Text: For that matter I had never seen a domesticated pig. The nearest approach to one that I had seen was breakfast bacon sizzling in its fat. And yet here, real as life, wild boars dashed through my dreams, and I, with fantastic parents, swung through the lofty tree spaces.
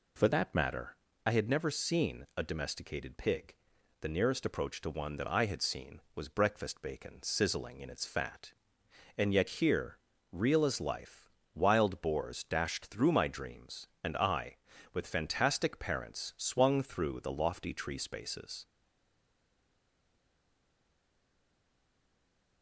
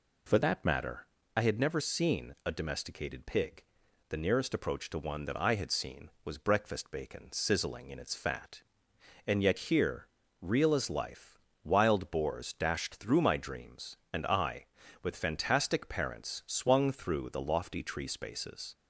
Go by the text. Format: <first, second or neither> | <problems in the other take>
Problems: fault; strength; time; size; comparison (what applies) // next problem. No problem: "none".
second | pauses between "matter" and "I"; slight; at 0.9 s; 0.30 s long; slight in the second // stays silent after the last word; strong; from 18.6 s on; 4.0 s long